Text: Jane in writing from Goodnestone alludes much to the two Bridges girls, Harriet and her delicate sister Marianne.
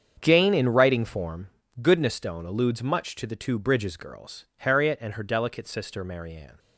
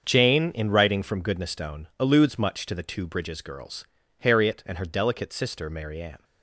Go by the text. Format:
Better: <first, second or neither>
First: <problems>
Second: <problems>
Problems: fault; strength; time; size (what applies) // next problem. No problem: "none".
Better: second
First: starts louder than the rest; strong; until 1.2 s; 7.5 dB // says "form" for "from"; at 1.0 s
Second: starts louder than the rest; until 1.0 s; 7 dB